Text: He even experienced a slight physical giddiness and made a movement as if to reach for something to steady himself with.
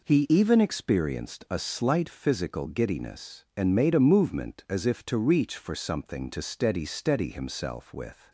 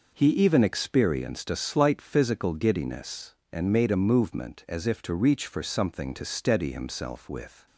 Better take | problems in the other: second | says "steady" twice; at 6.8 s

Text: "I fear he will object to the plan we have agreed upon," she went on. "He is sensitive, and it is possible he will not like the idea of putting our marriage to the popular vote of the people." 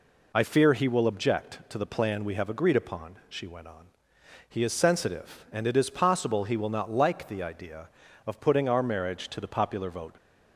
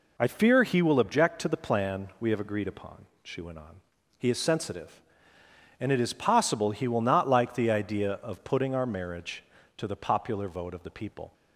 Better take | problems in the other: second | stops before "of the people"; at 10.1 s

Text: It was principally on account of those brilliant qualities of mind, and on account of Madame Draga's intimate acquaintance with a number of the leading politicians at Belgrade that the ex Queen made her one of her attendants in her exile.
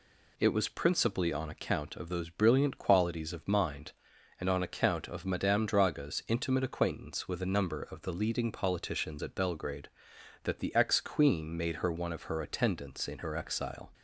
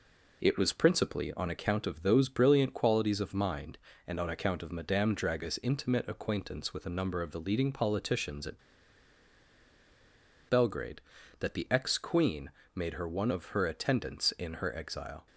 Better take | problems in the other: first | pauses between "at" and "Belgrade"; strong; at 8.5 s; 1.9 s long // pauses between "Queen" and "made"; slight; at 12.5 s; 0.22 s long

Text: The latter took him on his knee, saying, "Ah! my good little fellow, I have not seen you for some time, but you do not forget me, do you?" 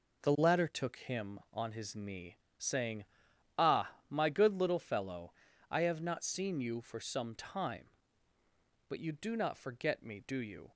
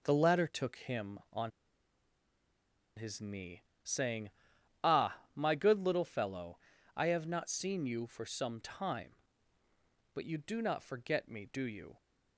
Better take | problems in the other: first | pauses between "on" and "his"; strong; at 1.5 s; 1.4 s long

